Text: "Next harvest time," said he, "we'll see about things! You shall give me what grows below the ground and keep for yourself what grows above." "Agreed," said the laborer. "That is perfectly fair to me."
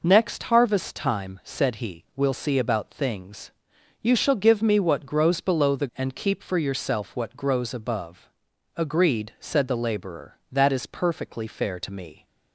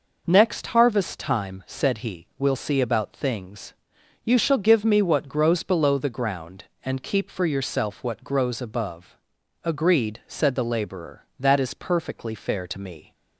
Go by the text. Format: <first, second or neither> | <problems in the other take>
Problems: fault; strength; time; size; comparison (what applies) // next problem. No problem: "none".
second | skips "ground"; at 5.9 s